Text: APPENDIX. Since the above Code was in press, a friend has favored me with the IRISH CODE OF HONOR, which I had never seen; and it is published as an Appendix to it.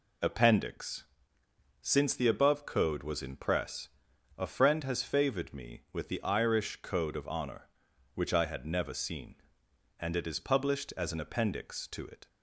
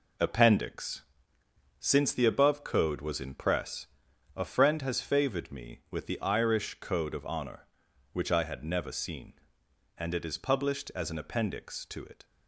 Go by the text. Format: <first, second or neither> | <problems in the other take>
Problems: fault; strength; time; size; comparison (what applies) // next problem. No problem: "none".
first | gets quieter; throughout; 7 dB